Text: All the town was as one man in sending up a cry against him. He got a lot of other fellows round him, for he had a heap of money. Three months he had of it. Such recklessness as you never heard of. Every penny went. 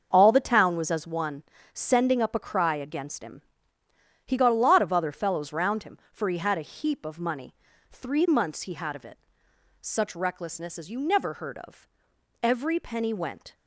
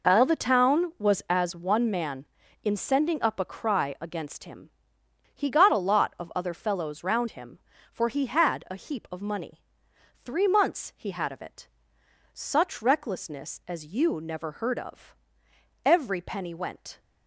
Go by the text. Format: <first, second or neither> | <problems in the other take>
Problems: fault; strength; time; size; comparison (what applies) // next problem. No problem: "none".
second | starts louder than the rest; until 1.1 s; 6.5 dB // skips "man in"; at 1.5 s